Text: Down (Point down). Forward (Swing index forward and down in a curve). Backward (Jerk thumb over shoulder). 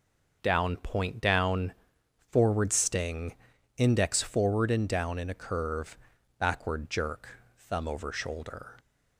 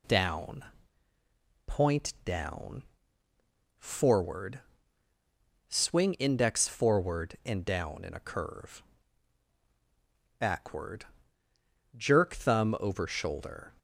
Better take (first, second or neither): second